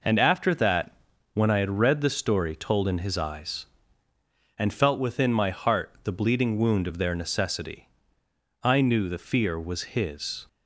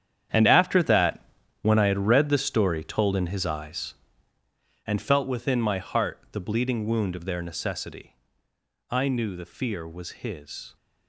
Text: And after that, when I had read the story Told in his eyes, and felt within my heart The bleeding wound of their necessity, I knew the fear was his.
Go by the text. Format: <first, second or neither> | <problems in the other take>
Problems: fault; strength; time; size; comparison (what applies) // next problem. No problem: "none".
first | gets quieter; strong; throughout; 13 dB